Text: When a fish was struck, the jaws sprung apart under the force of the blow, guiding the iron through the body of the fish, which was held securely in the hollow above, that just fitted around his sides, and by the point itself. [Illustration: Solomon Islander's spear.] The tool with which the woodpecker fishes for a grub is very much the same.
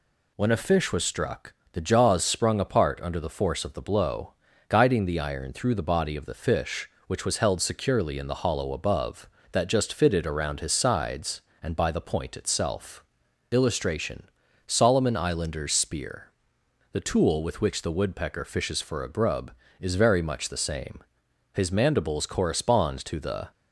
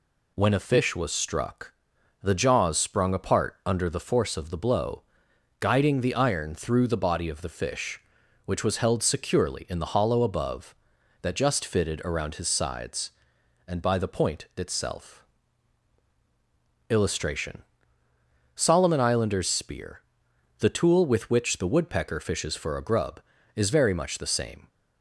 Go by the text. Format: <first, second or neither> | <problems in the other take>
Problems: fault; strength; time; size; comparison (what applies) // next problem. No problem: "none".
second | goes on to say "His mandibles correspond to the"; strong; from 21.5 s on; 1.9 s long